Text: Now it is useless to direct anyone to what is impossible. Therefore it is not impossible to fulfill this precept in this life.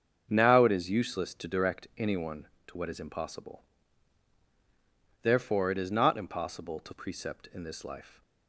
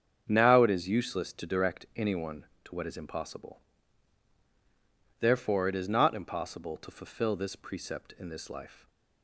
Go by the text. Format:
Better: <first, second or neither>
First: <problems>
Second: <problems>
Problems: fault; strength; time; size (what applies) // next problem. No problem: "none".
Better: second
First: starts louder than the rest; until 1.3 s; 7 dB // skips "fulfill this"; at 6.9 s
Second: starts louder than the rest; strong; until 1.2 s; 7.5 dB